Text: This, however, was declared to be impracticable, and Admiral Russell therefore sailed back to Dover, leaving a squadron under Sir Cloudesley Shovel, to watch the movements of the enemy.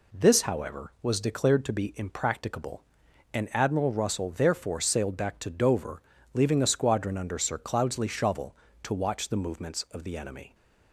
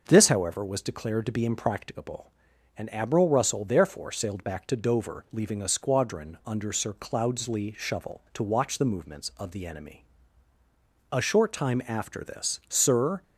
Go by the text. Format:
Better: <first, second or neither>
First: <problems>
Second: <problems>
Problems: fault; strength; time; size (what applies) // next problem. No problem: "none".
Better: first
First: none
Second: goes on to say "A short time after this Sir"; strong; from 11.1 s on; 2.1 s long